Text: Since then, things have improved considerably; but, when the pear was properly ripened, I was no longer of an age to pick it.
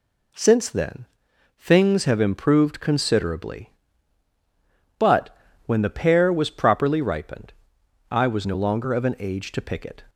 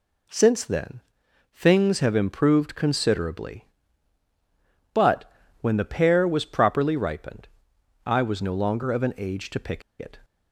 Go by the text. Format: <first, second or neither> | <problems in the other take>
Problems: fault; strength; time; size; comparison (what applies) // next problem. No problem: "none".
first | pauses between "pick" and "it"; slight; at 9.8 s; 0.20 s long